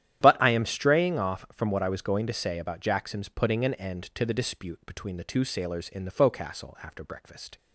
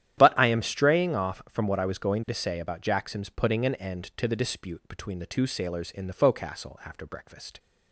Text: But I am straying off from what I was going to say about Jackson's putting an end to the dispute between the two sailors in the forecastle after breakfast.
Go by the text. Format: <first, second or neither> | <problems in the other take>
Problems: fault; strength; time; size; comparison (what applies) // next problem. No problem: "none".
neither | starts louder than the rest; strong; the same in both